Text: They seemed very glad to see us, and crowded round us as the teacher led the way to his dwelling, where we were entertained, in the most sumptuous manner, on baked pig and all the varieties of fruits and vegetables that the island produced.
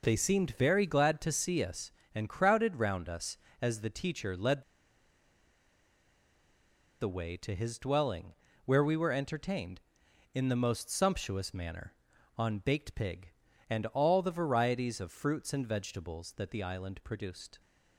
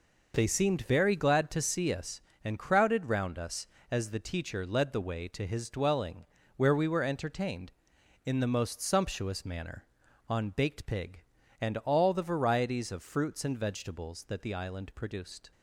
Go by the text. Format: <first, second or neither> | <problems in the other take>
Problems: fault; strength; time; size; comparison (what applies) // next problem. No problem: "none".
second | pauses between "led" and "the"; strong; at 4.6 s; 2.3 s long